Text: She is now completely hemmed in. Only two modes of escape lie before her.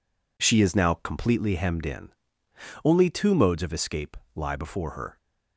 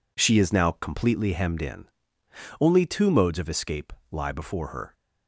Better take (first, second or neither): neither